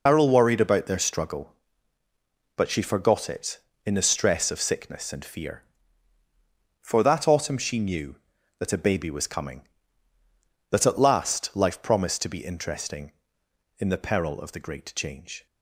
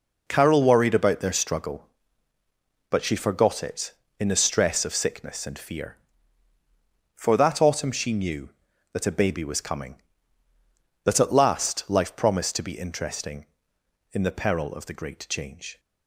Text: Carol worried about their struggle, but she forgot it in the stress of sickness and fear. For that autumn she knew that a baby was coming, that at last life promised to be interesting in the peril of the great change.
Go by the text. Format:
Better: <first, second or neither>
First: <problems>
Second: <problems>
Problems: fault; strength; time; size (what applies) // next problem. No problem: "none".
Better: second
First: loses the start of "Carol"; at 0.0 s; 115 ms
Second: none